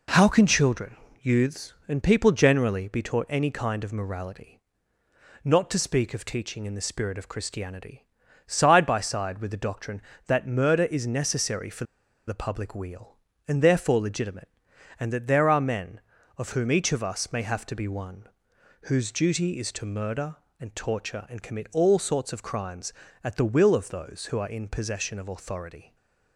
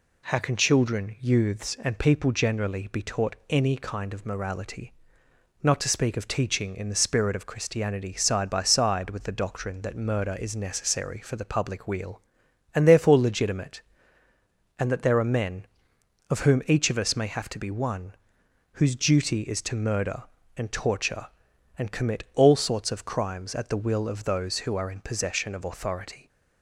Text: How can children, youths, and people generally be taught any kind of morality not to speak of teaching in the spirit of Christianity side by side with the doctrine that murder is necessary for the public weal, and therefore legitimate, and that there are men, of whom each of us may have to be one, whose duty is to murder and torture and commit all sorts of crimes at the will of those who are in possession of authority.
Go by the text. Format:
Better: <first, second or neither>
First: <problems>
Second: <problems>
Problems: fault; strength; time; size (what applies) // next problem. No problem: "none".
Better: second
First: pauses between "morality" and "not"; noticeable; at 4.5 s; 0.86 s long // pauses between "Christianity" and "side"; at 8.0 s; 0.40 s long // pauses between "for" and "the"; at 11.8 s; 0.42 s long // stays silent after the last word; slight; from 25.8 s on; 0.5 s long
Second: pauses between "morality" and "not"; noticeable; at 4.9 s; 0.68 s long